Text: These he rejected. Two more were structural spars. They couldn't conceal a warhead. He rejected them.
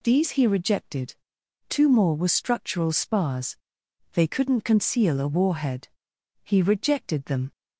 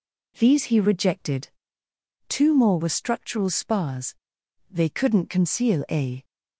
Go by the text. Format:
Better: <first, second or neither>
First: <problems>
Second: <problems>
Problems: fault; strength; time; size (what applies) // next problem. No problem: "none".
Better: first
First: none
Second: stops before "warhead He rejected them"; at 6.2 s